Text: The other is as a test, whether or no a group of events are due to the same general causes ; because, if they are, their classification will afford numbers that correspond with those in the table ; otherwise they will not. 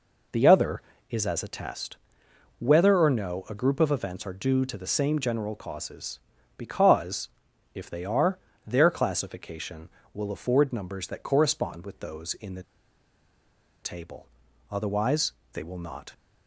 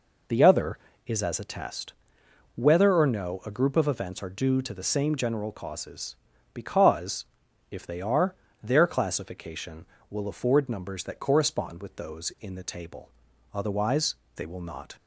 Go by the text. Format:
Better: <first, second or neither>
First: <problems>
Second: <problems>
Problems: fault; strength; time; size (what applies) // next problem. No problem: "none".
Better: second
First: pauses between "the" and "table"; at 12.6 s; 1.1 s long // pauses between "otherwise" and "they"; slight; at 15.3 s; 0.18 s long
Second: pauses between "otherwise" and "they"; slight; at 14.1 s; 0.18 s long